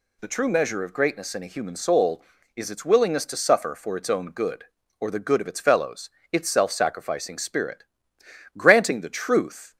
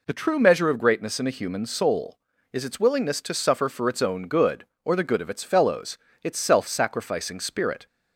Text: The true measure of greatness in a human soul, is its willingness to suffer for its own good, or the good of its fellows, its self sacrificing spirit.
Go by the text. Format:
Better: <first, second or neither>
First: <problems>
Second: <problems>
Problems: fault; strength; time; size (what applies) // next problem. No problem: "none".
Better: second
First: goes on to say "Granting the truth"; noticeable; from 8.5 s on; 1.2 s long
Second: none